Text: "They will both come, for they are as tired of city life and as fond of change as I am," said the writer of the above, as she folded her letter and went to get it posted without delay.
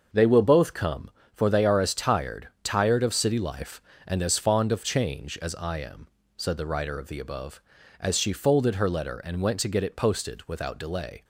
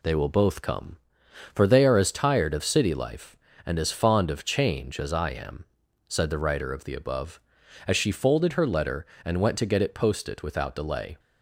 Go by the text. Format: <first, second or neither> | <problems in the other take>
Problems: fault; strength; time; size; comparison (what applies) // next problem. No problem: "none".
second | starts louder than the rest; until 1.3 s; 6 dB // says "tired" twice; at 2.6 s